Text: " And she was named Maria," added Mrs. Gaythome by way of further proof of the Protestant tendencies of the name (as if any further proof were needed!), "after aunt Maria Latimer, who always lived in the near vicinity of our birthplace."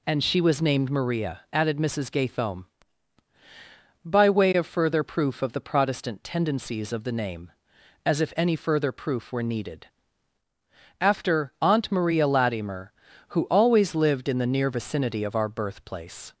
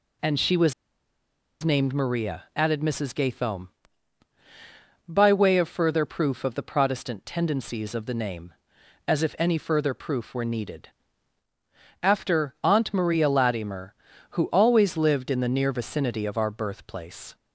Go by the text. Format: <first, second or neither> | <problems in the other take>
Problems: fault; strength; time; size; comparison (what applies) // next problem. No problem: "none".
first | pauses between "was" and "named"; noticeable; at 0.7 s; 0.90 s long